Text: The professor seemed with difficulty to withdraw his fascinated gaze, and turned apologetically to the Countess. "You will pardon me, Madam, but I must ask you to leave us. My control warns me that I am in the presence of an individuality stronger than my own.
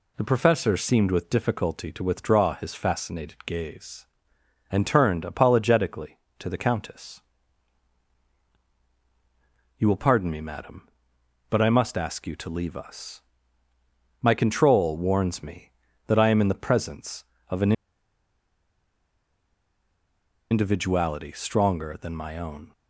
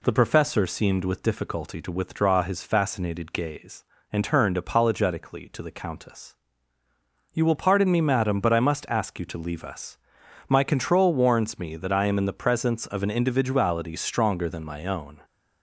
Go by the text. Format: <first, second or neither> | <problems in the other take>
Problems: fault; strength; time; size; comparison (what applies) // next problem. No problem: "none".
second | pauses between "an" and "individuality"; strong; at 17.7 s; 2.7 s long